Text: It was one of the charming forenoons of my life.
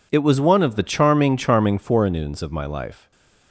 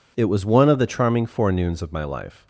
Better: second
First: says "charming" twice; at 1.3 s // stays silent after the last word; slight; from 2.9 s on; 0.6 s long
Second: none

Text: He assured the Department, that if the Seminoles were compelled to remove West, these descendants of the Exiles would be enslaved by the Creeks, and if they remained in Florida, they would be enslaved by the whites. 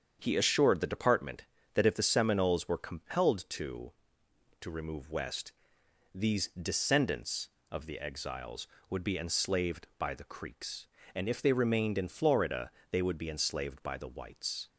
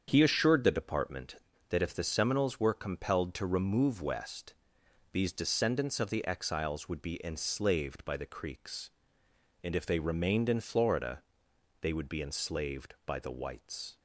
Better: second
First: starts louder than the rest; strong; until 1.2 s; 7.5 dB // says "to" twice; at 4.6 s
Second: starts louder than the rest; strong; until 1.0 s; 7.5 dB

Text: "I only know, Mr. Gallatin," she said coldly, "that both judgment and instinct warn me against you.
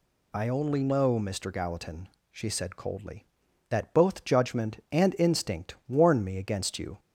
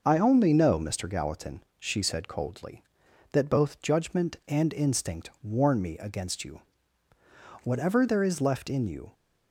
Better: first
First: none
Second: goes on to say "Whatever there is left in you"; from 7.6 s on; 1.4 s long

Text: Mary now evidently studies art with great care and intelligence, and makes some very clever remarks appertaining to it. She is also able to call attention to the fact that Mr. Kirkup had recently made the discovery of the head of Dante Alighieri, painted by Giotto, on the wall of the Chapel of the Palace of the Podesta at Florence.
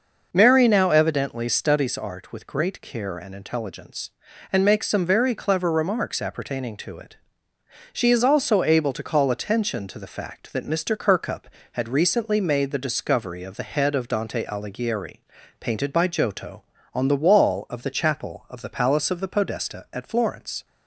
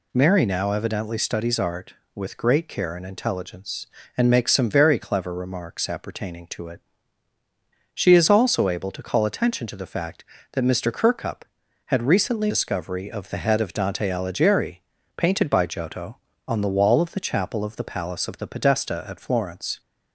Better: first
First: none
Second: skips "made the"; at 12.5 s

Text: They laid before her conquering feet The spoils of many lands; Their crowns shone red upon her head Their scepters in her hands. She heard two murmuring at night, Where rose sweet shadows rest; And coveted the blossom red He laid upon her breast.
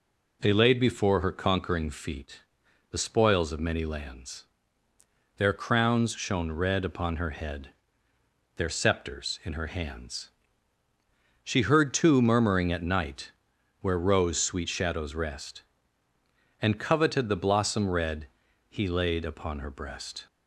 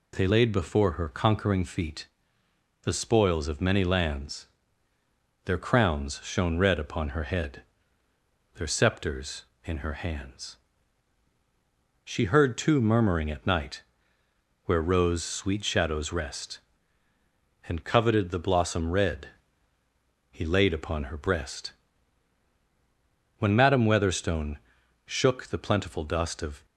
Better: first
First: pauses between "feet" and "The"; noticeable; at 2.4 s; 0.48 s long // pauses between "head" and "Their"; noticeable; at 7.7 s; 0.84 s long // pauses between "red" and "He"; at 18.2 s; 0.40 s long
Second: pauses between "feet" and "The"; noticeable; at 2.0 s; 0.76 s long // pauses between "head" and "Their"; noticeable; at 7.6 s; 0.92 s long // pauses between "red" and "He"; at 19.2 s; 1.0 s long // goes on to say "When Madam Weatherstone shook the plentiful dust of"; strong; from 23.3 s on; 3.2 s long

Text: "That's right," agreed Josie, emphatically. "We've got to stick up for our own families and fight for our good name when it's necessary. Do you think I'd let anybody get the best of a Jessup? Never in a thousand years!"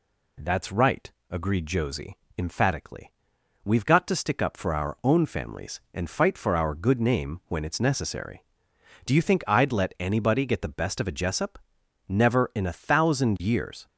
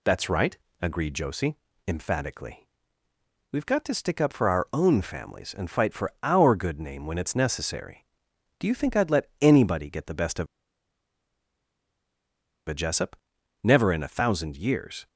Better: first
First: none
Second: pauses between "of" and "a"; strong; at 10.4 s; 2.2 s long

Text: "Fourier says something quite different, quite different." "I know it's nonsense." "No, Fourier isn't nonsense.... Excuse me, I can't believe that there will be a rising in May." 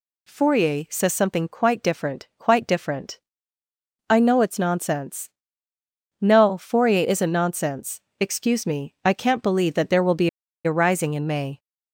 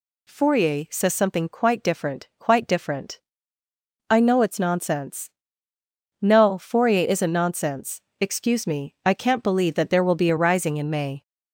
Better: second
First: pauses between "be" and "a"; at 10.2 s; 0.37 s long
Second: none

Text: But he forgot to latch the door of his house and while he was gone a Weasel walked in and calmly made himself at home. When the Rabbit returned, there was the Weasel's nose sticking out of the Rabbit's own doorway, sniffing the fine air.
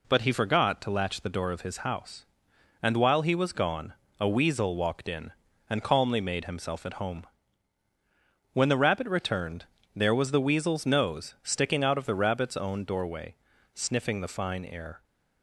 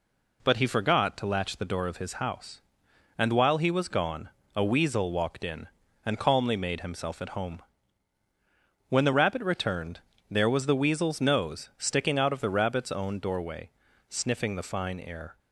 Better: neither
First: pauses between "gone" and "a"; slight; at 3.9 s; 0.26 s long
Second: pauses between "gone" and "a"; slight; at 4.2 s; 0.26 s long

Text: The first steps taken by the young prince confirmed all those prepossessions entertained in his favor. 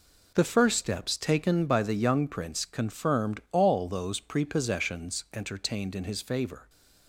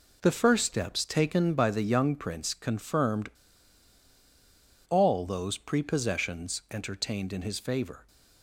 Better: first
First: none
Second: pauses between "confirmed" and "all"; strong; at 3.3 s; 1.5 s long

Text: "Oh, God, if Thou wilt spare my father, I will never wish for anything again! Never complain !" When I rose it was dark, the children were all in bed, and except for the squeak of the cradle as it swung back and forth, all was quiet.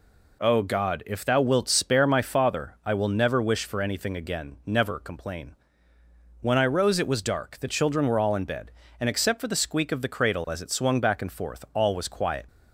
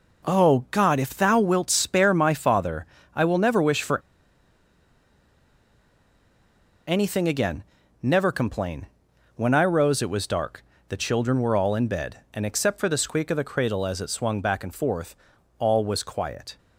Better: first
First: none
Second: pauses between "for" and "anything"; strong; at 4.0 s; 2.8 s long

